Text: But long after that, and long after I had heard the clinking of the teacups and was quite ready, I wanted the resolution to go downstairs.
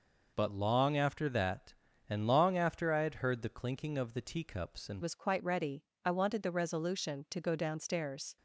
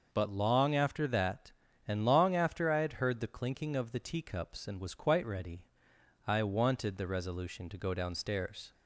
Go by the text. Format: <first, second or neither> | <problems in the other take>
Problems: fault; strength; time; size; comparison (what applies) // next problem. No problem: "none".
second | changes voice at "was"; from 5.0 s on; 3.3 s long